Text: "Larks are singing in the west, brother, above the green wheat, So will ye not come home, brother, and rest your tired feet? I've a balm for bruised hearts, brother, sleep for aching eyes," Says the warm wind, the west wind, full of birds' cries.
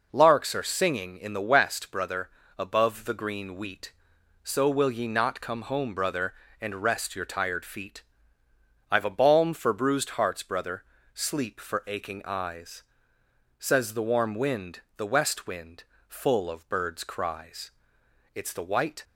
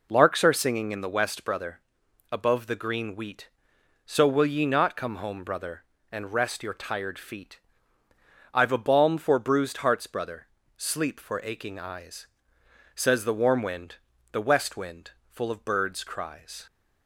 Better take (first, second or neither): second